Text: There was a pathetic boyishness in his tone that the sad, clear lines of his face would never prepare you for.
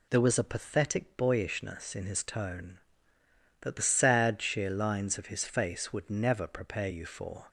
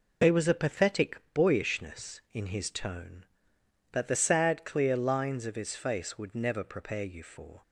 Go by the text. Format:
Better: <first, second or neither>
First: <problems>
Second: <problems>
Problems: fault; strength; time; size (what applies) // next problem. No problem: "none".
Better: second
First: says "sheer" for "clear"; at 4.3 s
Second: none